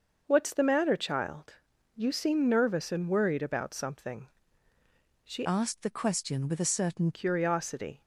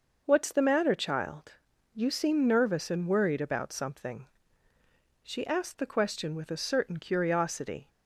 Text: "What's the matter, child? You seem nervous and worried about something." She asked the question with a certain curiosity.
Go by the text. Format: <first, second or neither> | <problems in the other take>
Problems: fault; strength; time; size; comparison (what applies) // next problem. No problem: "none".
second | starts louder than the rest; noticeable; until 1.2 s; 6 dB // changes voice from "asked" to "certain"; from 5.4 to 7.1 s; 1.7 s long